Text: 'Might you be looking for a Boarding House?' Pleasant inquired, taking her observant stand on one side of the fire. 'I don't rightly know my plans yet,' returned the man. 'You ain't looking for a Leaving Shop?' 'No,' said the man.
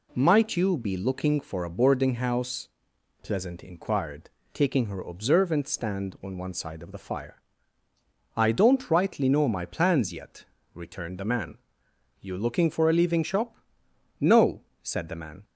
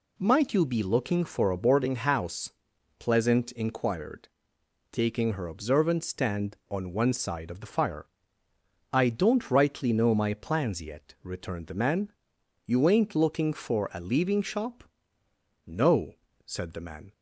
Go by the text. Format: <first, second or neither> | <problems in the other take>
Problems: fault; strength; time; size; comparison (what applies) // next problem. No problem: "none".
second | skips "ain't"; at 12.3 s